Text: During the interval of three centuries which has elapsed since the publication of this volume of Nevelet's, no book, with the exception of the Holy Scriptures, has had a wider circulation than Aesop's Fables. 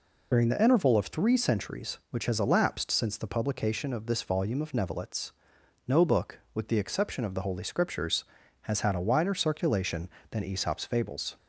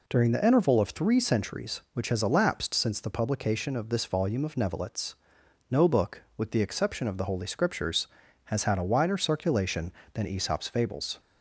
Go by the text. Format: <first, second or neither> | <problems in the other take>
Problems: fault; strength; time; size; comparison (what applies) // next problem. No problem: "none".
second | loses the start of "During"; at 0.3 s; 70 ms